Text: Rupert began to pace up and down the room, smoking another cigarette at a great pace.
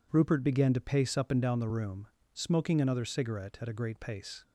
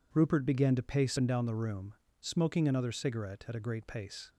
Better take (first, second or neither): first